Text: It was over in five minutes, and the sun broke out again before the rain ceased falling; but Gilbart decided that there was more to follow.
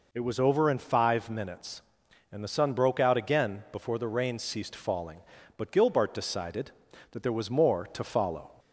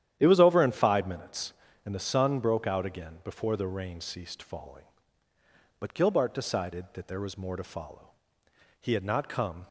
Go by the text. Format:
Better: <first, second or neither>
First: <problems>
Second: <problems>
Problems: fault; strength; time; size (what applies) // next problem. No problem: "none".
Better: first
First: none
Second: starts louder than the rest; strong; until 1.2 s; 10.5 dB // goes on to say "He had not come"; noticeable; from 8.8 s on; 0.86 s long